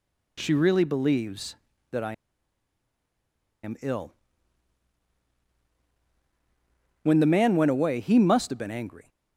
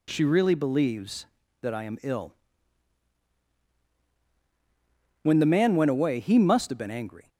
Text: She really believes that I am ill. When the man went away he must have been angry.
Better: second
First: pauses between "I" and "am"; strong; at 2.1 s; 1.5 s long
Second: none

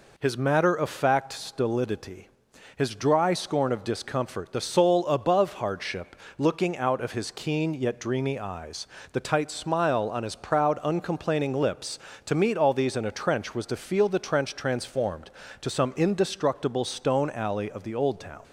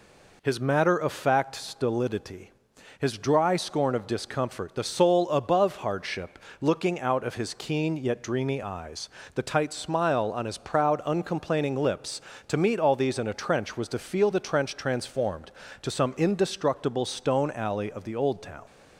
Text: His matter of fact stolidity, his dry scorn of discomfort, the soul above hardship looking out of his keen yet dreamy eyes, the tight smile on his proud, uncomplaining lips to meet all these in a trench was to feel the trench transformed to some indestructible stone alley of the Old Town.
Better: neither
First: pauses between "hardship" and "looking"; slight; at 6.1 s; 0.22 s long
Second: pauses between "hardship" and "looking"; slight; at 6.3 s; 0.22 s long

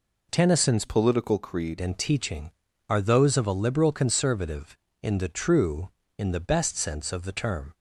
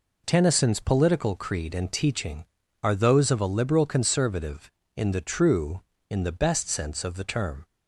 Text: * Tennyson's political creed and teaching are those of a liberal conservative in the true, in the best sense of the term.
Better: second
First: changes voice from "political" to "creed"; from 0.8 to 1.7 s; 0.9 s long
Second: none

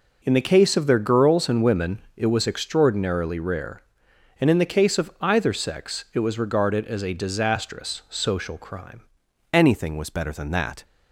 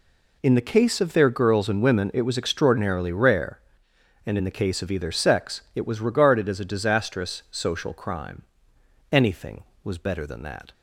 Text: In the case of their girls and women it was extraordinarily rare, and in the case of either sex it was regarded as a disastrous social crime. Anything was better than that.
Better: second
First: pauses between "women" and "it"; slight; at 1.9 s; 0.16 s long // changes voice at "Anything"; from 9.5 s on; 1.3 s long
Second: none

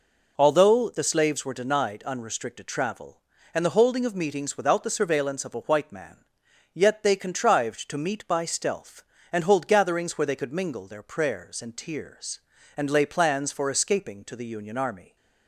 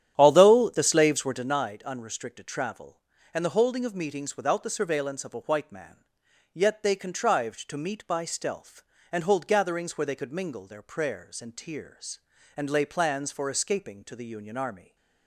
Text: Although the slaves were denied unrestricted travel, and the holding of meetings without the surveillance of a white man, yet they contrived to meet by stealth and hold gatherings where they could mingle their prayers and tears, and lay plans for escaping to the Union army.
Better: first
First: none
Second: starts louder than the rest; strong; until 1.6 s; 10 dB

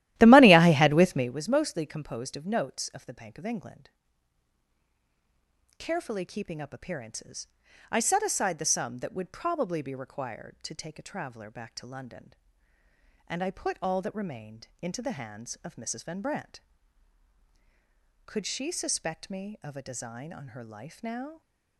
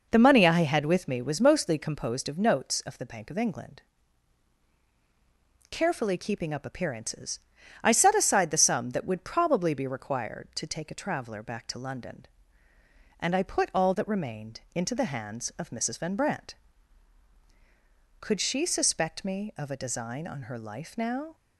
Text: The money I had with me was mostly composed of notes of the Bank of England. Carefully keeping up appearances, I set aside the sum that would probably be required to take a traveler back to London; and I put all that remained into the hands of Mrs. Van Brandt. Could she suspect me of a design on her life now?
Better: second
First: starts louder than the rest; strong; until 1.4 s; 14.5 dB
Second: none

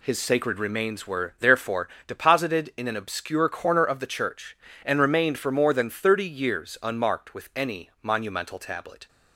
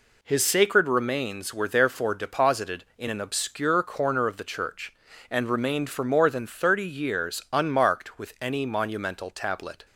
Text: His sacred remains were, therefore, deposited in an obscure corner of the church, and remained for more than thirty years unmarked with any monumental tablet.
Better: neither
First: none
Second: none

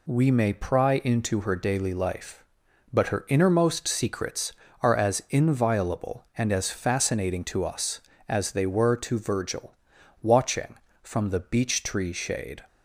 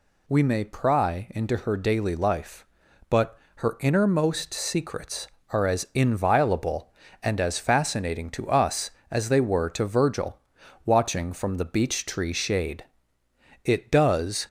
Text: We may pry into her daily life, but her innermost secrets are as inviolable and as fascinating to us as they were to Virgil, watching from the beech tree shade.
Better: first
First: none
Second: pauses between "but" and "her"; slight; at 3.3 s; 0.18 s long // goes on to say "It does"; noticeable; from 13.6 s on; 0.82 s long

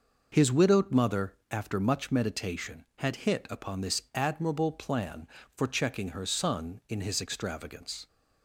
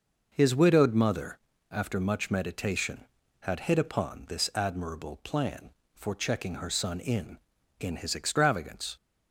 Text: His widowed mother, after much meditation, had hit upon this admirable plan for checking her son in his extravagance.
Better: first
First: none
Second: says "in" twice; at 7.7 s

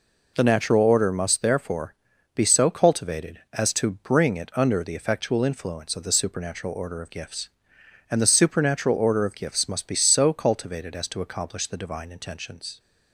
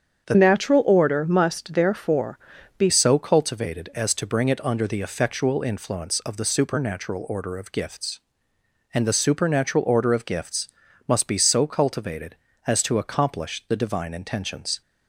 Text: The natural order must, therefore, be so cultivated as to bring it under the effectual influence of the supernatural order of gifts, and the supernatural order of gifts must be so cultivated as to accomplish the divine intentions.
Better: first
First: none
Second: starts louder than the rest; strong; until 1.3 s; 7.5 dB // changes voice from "natural" to "be"; from 0.3 to 2.8 s; 2.5 s long // pauses between "gifts" and "must"; at 10.6 s; 0.38 s long

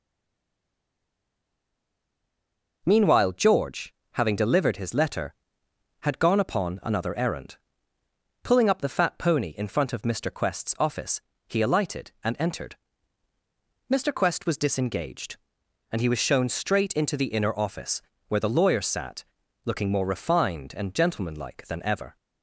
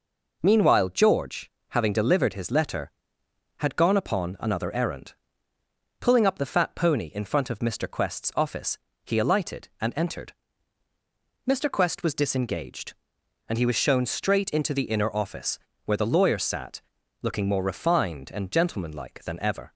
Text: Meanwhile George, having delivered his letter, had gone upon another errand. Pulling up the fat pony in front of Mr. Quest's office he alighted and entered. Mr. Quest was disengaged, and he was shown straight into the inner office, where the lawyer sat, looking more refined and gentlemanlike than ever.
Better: second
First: stays silent before the first word; strong; until 2.8 s; 2.8 s long // pauses between "office" and "he"; slight; at 11.2 s; 0.26 s long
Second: pauses between "office" and "he"; slight; at 8.7 s; 0.26 s long

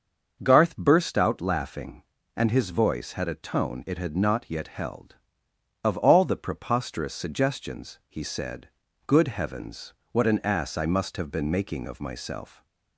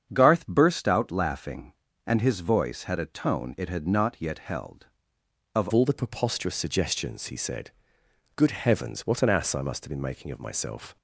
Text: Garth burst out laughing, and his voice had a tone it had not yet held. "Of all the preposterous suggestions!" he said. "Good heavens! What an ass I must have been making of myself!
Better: first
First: starts louder than the rest; until 1.4 s; 6.5 dB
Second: starts louder than the rest; strong; until 1.1 s; 8 dB // changes voice at "all"; from 5.7 s on; 5.2 s long

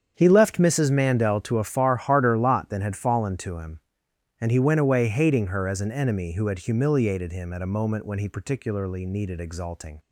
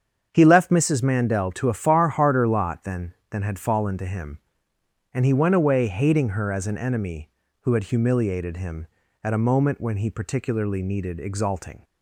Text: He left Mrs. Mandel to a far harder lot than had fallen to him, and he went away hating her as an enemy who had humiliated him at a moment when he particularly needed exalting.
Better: first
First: starts louder than the rest; strong; until 1.1 s; 8 dB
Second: starts louder than the rest; strong; until 1.3 s; 7.5 dB // says "than" twice; at 3.2 s

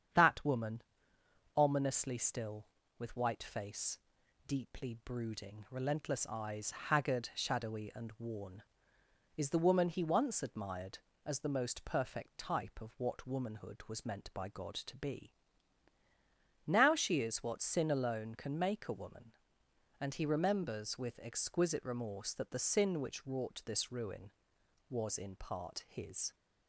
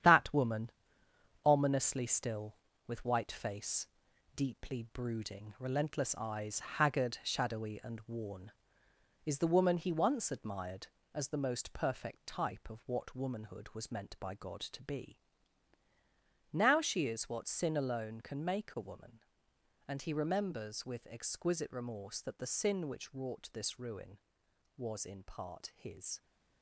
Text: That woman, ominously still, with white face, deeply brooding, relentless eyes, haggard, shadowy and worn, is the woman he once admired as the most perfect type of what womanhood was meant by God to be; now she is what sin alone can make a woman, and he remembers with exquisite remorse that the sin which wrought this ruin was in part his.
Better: first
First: starts louder than the rest; strong; until 1.8 s; 8 dB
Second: gets quieter; throughout; 7 dB // starts louder than the rest; strong; until 1.7 s; 9.5 dB

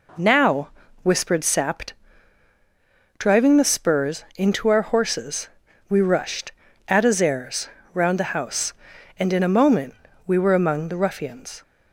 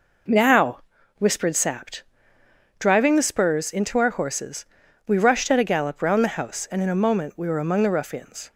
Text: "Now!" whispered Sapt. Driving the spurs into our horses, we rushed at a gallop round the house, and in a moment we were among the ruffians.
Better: second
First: says "zares" for "gallop"; at 7.1 s // pauses between "moment" and "we"; slight; at 9.9 s; 0.32 s long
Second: none

